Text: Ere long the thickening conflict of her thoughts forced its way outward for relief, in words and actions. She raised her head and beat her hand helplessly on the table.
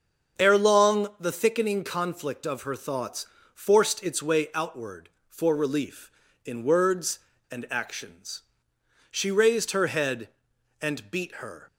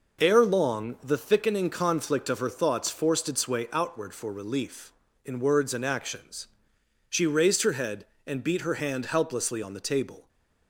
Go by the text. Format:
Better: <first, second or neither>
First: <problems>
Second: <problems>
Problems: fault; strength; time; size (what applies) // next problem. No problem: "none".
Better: second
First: starts louder than the rest; until 1.4 s; 6.5 dB // pauses between "thoughts" and "forced"; slight; at 3.2 s; 0.28 s long // stops before "hand helplessly on the table"; at 11.6 s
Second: none